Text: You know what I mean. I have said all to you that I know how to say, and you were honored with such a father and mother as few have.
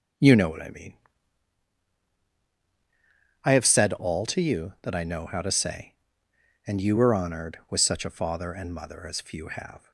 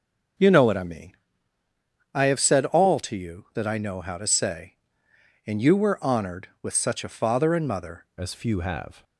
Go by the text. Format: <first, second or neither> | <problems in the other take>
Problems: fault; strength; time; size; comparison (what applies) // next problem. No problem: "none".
first | starts louder than the rest; until 2.3 s; 6 dB; also in the first // changes voice at "as"; from 8.1 s on; 0.9 s long